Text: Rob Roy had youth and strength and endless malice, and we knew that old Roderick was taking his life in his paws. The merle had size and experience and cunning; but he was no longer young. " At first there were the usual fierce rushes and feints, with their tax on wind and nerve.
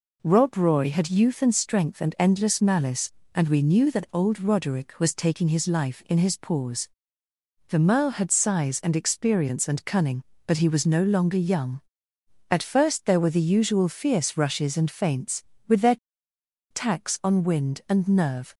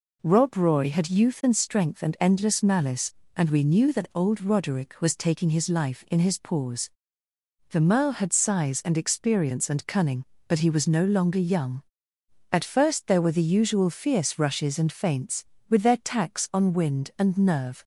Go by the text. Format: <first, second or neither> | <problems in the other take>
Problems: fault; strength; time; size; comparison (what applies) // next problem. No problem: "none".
second | pauses between "their" and "tax"; noticeable; at 15.9 s; 0.74 s long